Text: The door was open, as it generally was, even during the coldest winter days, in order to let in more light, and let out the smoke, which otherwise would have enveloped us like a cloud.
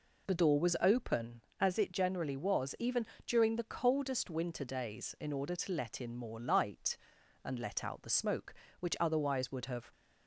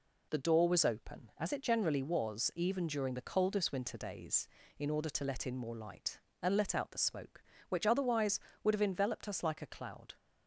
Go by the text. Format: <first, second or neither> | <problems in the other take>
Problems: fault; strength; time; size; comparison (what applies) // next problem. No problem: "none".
second | pauses between "even" and "during"; slight; at 3.0 s; 0.22 s long // stops before "enveloped us like a cloud"; at 9.9 s